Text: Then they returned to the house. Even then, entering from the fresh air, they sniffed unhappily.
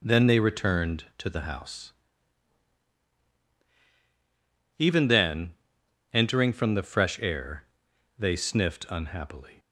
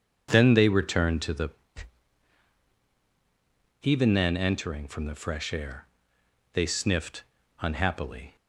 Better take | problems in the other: first | skips "house"; at 2.6 s // pauses between "sniffed" and "unhappily"; at 7.2 s; 0.38 s long

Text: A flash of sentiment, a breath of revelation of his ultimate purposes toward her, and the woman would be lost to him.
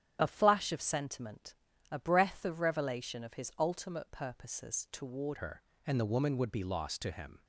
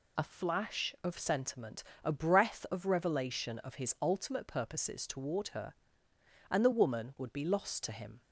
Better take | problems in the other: second | starts louder than the rest; strong; until 1.2 s; 10 dB // changes voice at "her"; from 5.3 s on; 2.1 s long

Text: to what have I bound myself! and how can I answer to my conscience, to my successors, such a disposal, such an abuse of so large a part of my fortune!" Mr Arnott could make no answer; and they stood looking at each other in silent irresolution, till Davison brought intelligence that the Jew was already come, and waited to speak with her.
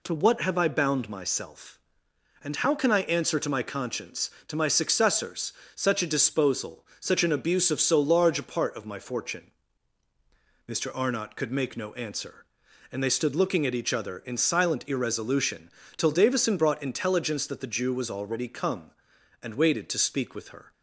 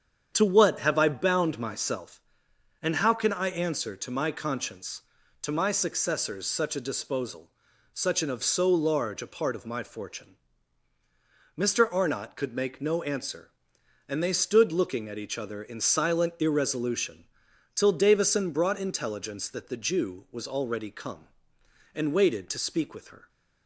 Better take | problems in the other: first | starts louder than the rest; strong; until 1.3 s; 8 dB // skips "abuse"; at 8.2 s

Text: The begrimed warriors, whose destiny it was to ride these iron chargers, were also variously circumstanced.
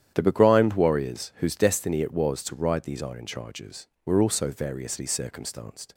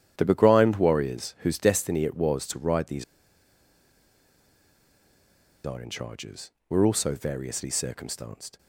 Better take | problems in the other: first | starts louder than the rest; strong; until 1.1 s; 10 dB; strong in the first // pauses between "these" and "iron"; strong; at 3.0 s; 2.6 s long

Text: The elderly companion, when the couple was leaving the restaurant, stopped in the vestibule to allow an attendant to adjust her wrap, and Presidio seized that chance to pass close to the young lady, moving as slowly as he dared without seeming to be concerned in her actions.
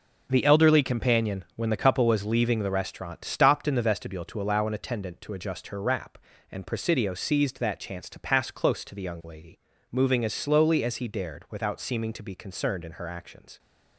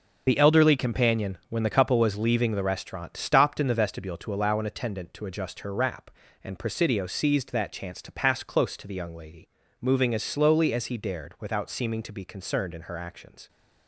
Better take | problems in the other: first | loses the start of "The"; at 0.2 s; 45 ms

